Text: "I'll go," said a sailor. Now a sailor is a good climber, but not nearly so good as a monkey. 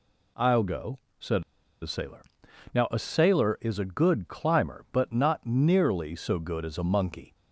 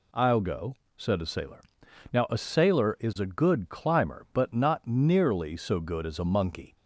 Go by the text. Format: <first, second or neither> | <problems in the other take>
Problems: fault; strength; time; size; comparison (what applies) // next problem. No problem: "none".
second | pauses between "said" and "a"; at 1.4 s; 0.39 s long